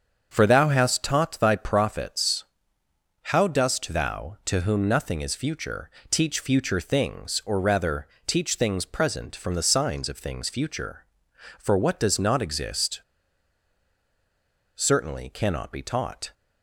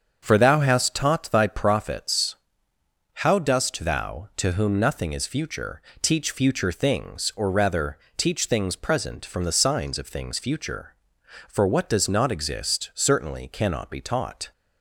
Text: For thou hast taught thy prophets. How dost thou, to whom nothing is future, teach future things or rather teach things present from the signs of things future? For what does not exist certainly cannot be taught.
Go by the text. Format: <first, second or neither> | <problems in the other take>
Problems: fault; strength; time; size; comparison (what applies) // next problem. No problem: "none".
second | starts louder than the rest; until 1.3 s; 7 dB; also in the second // pauses between "rather" and "teach"; slight; at 8.0 s; 0.20 s long; slight in the second // pauses between "exist" and "certainly"; strong; at 13.0 s; 1.7 s long